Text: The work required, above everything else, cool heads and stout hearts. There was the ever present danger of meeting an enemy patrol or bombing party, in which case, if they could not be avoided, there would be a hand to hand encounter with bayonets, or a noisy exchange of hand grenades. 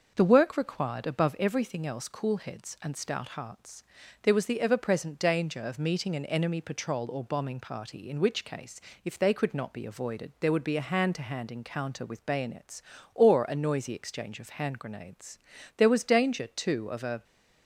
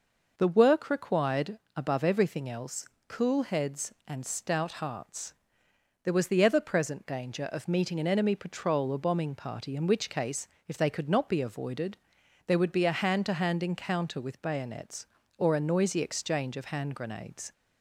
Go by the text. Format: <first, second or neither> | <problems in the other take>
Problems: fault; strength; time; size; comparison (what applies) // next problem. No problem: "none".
second | starts louder than the rest; noticeable; until 1.1 s; 6 dB // goes on to say "There was danger too of a"; from 15.7 s on; 1.4 s long